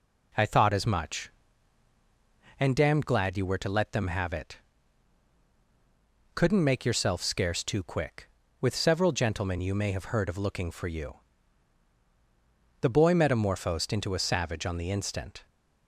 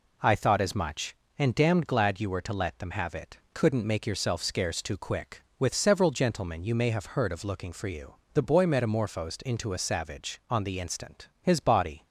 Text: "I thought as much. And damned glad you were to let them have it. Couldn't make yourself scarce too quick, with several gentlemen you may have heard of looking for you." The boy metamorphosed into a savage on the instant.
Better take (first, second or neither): first